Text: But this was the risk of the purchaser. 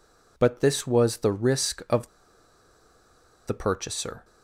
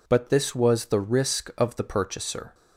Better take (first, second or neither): second